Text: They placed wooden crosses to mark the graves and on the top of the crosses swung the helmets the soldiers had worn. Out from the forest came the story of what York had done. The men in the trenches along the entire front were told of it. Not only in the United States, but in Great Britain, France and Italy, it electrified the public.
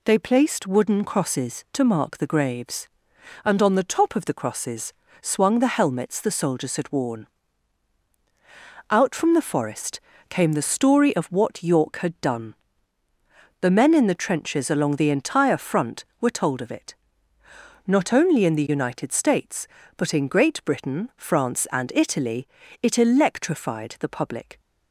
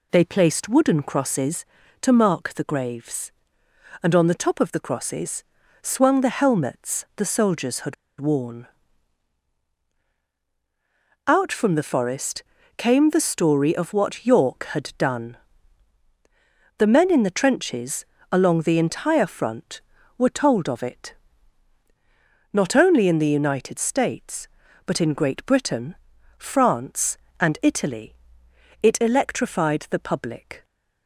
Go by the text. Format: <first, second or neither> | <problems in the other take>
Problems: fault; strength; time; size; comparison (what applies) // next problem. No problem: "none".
first | pauses between "crosses" and "swung"; at 5.4 s; 0.40 s long; slight in the first // pauses between "had" and "worn"; slight; at 7.9 s; 0.25 s long // pauses between "forest" and "came"; slight; at 12.4 s; 0.34 s long; slight in the first // pauses between "trenches" and "along"; slight; at 18.0 s; 0.28 s long